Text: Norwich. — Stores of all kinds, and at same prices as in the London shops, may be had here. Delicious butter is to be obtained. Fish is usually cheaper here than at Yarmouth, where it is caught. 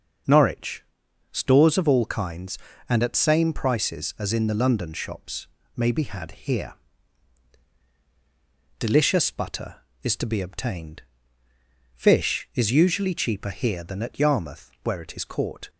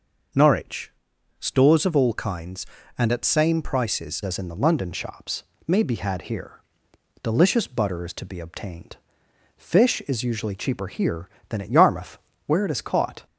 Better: first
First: starts louder than the rest; until 1.7 s; 6.5 dB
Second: starts louder than the rest; noticeable; until 1.8 s; 6 dB // changes voice at "as"; from 4.2 s on; 9.0 s long

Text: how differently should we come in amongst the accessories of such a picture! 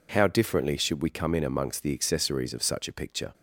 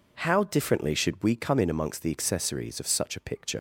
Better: first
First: none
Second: leaves "picture" unfinished; at 3.5 s; 70 ms

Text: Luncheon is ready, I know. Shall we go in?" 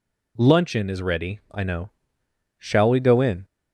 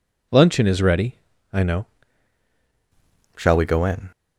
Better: first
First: none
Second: changes voice at "Shall"; from 3.3 s on; 0.7 s long

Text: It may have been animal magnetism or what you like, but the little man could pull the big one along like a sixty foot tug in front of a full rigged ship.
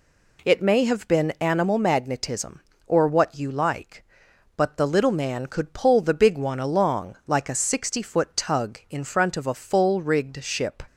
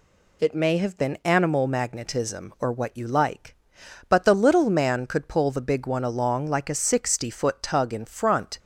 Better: first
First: none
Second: stops before "of a full rigged ship"; at 8.5 s

